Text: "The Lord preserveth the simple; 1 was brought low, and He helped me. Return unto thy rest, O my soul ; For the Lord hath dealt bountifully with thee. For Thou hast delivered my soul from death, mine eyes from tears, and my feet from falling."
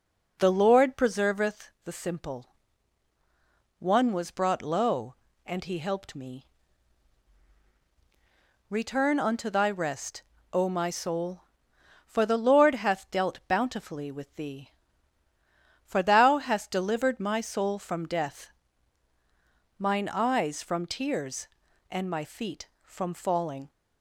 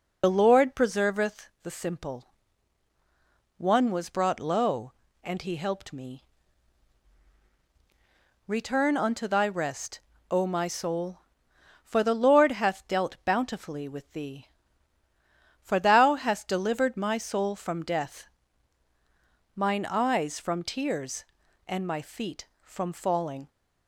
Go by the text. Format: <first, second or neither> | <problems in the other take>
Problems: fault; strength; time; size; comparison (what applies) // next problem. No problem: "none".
first | loses the start of "The"; at 0.2 s; 55 ms